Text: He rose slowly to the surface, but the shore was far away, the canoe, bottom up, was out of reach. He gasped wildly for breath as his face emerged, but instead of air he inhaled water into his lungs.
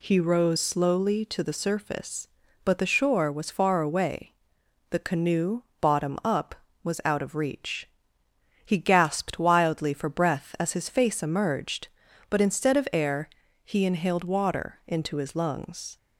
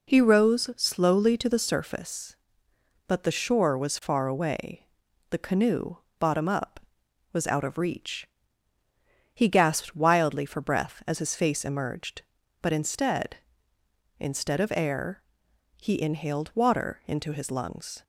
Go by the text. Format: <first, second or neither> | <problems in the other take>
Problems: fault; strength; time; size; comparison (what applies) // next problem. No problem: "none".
first | says "instead" twice; at 14.1 s // pauses between "air" and "he"; noticeable; at 15.2 s; 0.58 s long; slight in the first